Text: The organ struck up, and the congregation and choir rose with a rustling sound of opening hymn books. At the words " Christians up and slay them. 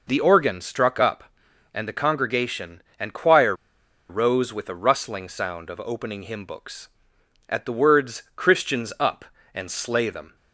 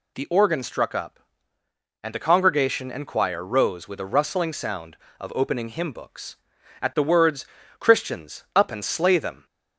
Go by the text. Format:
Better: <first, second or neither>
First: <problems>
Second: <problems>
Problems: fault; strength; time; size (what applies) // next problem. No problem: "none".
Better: second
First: pauses between "choir" and "rose"; noticeable; at 3.5 s; 0.55 s long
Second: none